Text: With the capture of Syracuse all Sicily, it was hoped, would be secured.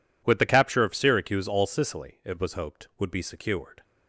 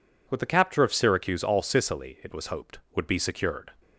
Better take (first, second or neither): neither